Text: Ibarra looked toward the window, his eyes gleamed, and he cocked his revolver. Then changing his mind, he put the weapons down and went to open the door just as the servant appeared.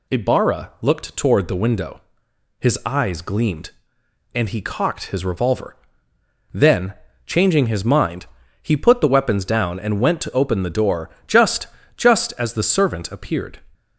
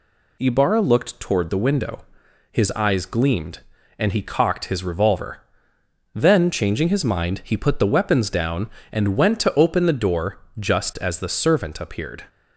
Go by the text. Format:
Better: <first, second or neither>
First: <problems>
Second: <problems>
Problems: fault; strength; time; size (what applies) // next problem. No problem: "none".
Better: second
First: pauses between "Then" and "changing"; slight; at 6.9 s; 0.32 s long // pauses between "door" and "just"; slight; at 11.0 s; 0.16 s long // says "just" twice; at 11.9 s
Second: pauses between "door" and "just"; slight; at 10.3 s; 0.20 s long